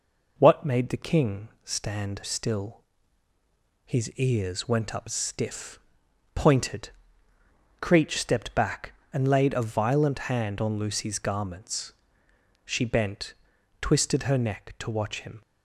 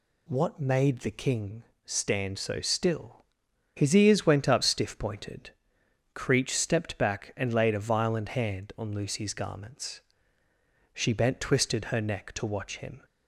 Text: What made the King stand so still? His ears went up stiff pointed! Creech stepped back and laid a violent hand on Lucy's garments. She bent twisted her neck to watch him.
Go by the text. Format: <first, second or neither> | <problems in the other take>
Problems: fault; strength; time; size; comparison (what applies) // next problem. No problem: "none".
second | pauses between "King" and "stand"; slight; at 1.4 s; 0.16 s long; slight in the second // skips "so"; at 2.2 s // pauses between "stiff" and "pointed"; noticeable; at 5.7 s; 0.54 s long // pauses between "bent" and "twisted"; noticeable; at 13.3 s; 0.48 s long